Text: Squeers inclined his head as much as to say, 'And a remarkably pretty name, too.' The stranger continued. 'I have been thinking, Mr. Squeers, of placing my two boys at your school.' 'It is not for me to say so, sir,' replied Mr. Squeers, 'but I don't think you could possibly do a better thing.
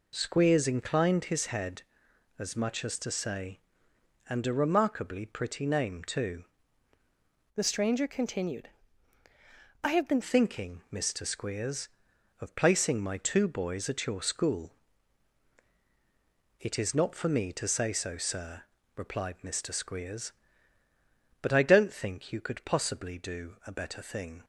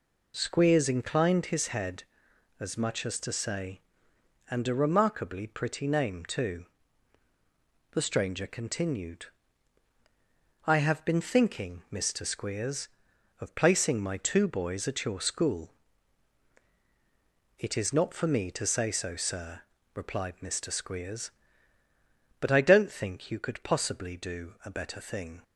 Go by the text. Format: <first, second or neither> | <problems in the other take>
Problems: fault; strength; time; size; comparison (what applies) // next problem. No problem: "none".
second | changes voice from "The" to "been"; from 7.5 to 10.2 s; 2.7 s long